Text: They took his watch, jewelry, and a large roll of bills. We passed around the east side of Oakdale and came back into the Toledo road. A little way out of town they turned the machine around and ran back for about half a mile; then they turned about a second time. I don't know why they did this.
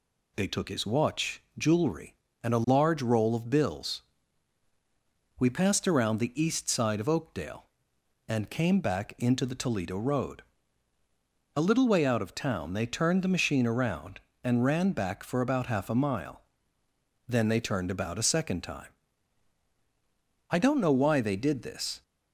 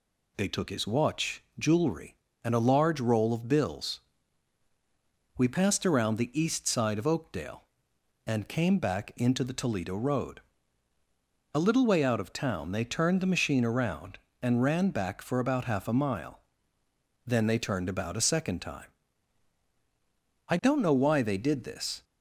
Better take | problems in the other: neither | none

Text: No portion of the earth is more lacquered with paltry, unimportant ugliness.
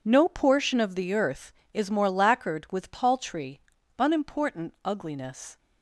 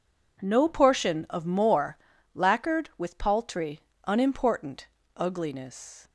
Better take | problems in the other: first | skips "the earth is"; at 1.4 s // pauses between "more" and "lacquered"; at 1.9 s; 0.38 s long // pauses between "unimportant" and "ugliness"; slight; at 4.8 s; 0.30 s long

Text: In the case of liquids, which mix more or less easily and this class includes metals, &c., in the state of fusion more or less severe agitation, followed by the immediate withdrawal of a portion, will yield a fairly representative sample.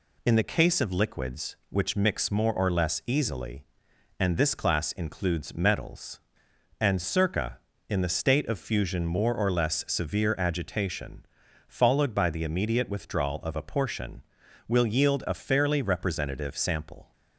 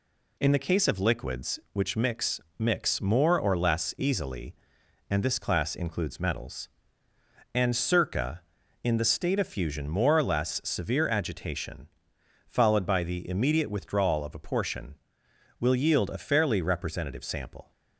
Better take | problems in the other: first | says "mix" twice; at 2.5 s

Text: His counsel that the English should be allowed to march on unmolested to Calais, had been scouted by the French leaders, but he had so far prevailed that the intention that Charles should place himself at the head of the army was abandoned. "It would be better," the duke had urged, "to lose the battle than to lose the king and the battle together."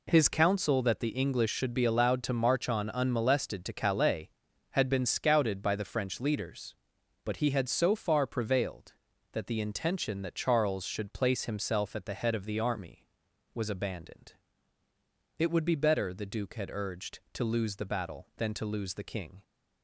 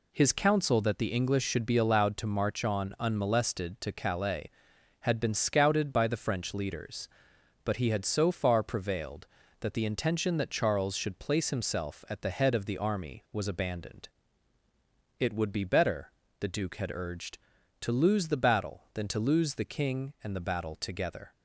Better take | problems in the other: second | stops before "and the battle together"; at 19.4 s

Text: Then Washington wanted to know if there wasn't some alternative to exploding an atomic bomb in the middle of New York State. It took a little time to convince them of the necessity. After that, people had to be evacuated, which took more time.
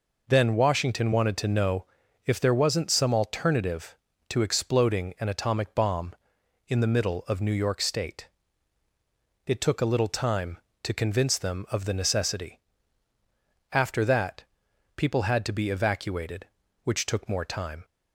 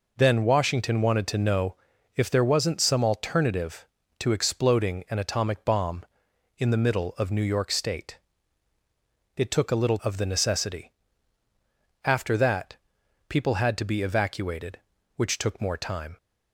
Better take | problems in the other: first | pauses between "know" and "if"; at 1.7 s; 0.40 s long; also in the first // skips "time to convince them"; at 9.9 s

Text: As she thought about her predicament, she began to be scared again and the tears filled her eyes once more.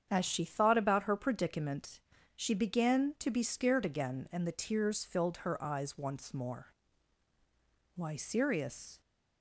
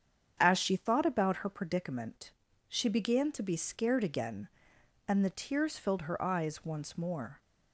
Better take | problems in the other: second | starts louder than the rest; strong; until 1.1 s; 8 dB; strong in the second // goes on to say "Why Sirius"; noticeable; from 7.9 s on; 1.0 s long

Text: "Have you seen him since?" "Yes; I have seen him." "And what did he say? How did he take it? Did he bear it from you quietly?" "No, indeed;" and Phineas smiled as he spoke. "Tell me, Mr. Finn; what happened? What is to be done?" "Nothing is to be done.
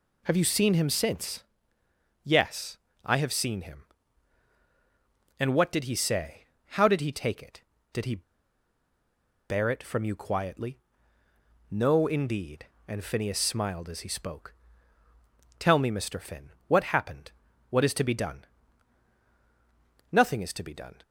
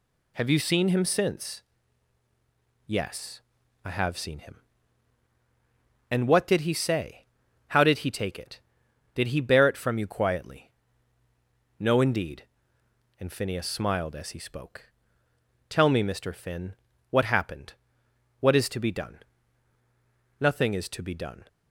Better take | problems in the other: second | pauses between "he" and "bear"; strong; at 8.2 s; 1.2 s long

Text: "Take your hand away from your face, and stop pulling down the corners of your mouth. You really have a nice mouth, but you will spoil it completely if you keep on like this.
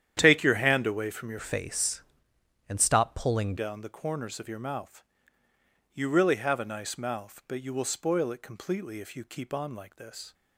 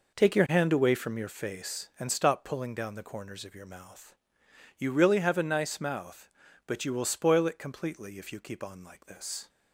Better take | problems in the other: second | starts louder than the rest; strong; until 1.1 s; 10 dB // changes voice from "face" to "pulling"; from 1.4 to 3.5 s; 2.1 s long

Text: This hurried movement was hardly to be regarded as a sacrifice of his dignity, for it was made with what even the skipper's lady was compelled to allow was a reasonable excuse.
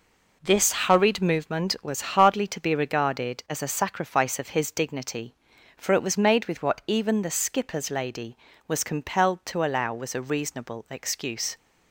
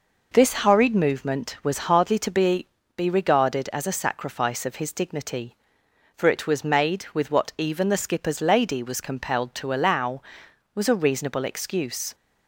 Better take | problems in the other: first | says "be" twice; at 2.9 s

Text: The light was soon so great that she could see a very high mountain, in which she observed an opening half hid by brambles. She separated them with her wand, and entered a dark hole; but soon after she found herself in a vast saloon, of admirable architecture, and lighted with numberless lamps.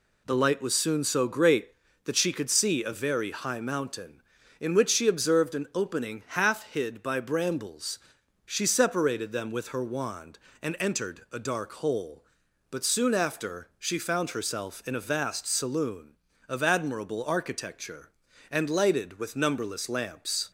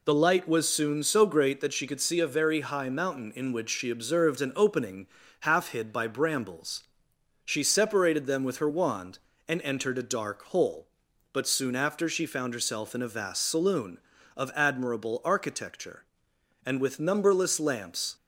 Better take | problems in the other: first | pauses between "opening" and "half"; slight; at 5.0 s; 0.34 s long // skips "lighted"; at 16.8 s

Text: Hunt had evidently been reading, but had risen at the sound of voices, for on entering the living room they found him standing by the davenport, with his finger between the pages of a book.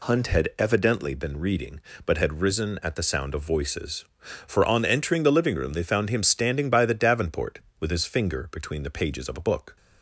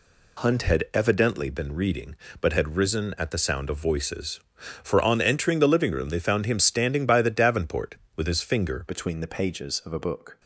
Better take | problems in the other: first | changes voice at "between"; from 8.8 s on; 1.5 s long

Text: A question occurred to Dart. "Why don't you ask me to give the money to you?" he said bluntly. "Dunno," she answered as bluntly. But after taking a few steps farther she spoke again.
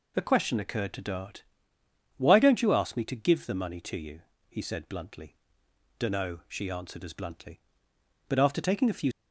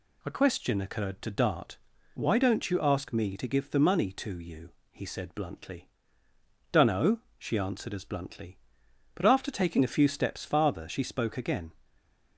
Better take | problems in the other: second | stops before "steps farther she spoke again"; at 9.1 s

